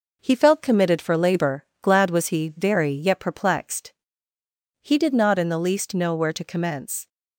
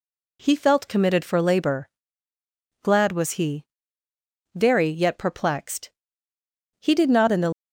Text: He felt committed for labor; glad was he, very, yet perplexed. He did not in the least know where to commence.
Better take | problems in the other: first | stops before "least know where to commence"; at 7.5 s

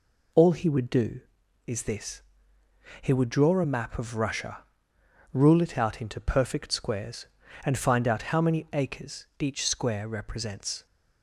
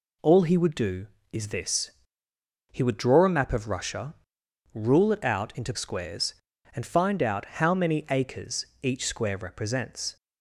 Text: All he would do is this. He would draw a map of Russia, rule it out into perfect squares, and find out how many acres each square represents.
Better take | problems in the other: first | skips "perfect"; at 5.7 s // pauses between "acres" and "each"; slight; at 8.6 s; 0.16 s long

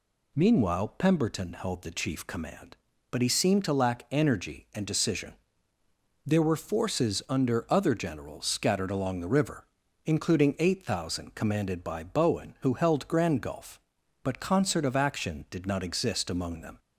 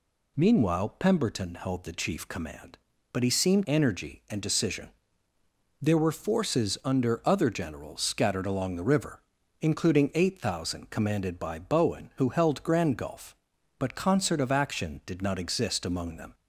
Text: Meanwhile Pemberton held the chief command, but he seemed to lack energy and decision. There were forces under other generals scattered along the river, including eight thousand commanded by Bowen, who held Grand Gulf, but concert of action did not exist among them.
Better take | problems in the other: first | skips "to lack"; at 3.6 s

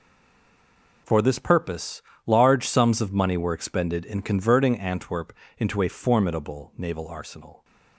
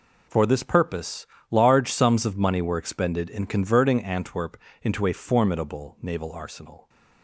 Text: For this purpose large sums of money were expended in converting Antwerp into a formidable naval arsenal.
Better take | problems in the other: second | stays silent before the first word; until 1.0 s; 1.0 s long // pauses between "purpose" and "large"; slight; at 2.0 s; 0.26 s long; slight in the second // pauses between "Antwerp" and "into"; slight; at 5.3 s; 0.28 s long; slight in the second

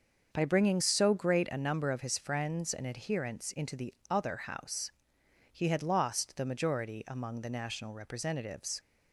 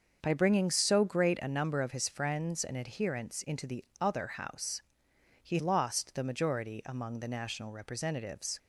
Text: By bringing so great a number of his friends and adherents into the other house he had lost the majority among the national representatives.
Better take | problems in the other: first | starts louder than the rest; until 1.2 s; 6.5 dB; also in the first // pauses between "the" and "other"; slight; at 3.8 s; 0.16 s long; slight in the first // pauses between "house" and "he"; noticeable; at 4.8 s; 0.60 s long; noticeable in the first // skips "had"; at 5.5 s

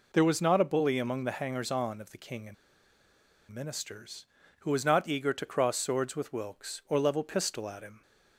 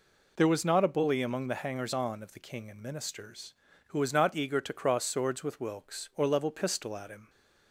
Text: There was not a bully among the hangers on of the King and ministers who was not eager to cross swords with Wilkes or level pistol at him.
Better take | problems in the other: second | pauses between "and" and "ministers"; noticeable; at 2.5 s; 0.96 s long

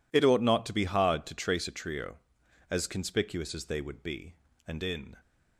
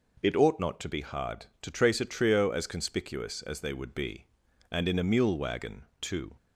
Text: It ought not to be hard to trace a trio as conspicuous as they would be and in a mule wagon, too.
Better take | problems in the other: second | stops before "a mule wagon too"; at 5.2 s

